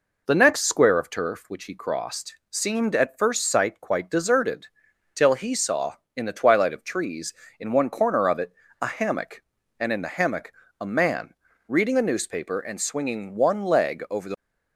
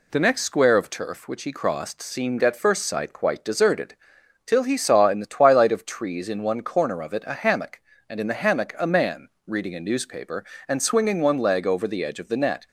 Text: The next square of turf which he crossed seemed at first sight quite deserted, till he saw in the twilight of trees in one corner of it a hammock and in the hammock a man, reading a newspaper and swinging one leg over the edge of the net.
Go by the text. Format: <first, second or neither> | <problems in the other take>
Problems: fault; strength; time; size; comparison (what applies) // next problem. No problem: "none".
second | pauses between "it" and "a"; slight; at 8.5 s; 0.30 s long // pauses between "hammock" and "a"; slight; at 10.5 s; 0.28 s long // stops before "edge of the net"; at 14.3 s